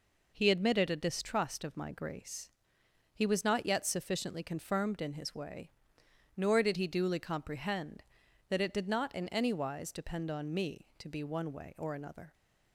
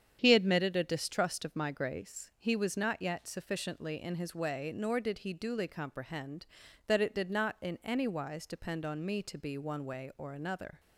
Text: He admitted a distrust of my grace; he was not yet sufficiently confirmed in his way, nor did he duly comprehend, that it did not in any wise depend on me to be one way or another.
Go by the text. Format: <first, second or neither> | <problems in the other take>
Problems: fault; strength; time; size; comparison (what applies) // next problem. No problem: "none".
first | starts louder than the rest; strong; until 1.2 s; 8.5 dB // skips "confirmed"; at 4.0 s